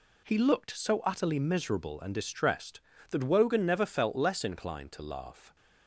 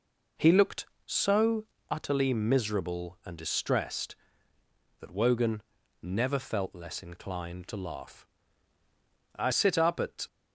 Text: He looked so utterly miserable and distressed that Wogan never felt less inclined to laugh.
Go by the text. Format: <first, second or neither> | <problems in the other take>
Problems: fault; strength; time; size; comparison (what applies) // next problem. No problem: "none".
first | pauses between "so" and "utterly"; slight; at 1.6 s; 0.26 s long // pauses between "Wogan" and "never"; at 5.6 s; 0.40 s long // goes on to say "I sit up at"; noticeable; from 9.3 s on; 0.88 s long